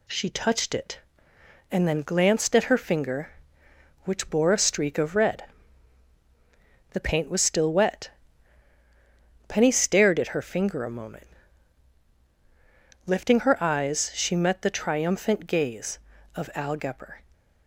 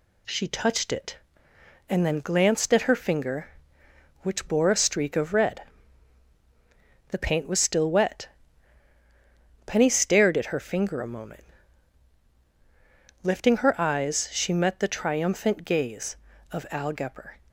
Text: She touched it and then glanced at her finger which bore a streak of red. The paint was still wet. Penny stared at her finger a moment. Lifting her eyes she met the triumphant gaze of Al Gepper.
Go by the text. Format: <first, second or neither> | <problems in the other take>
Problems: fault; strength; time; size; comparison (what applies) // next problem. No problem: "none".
neither | none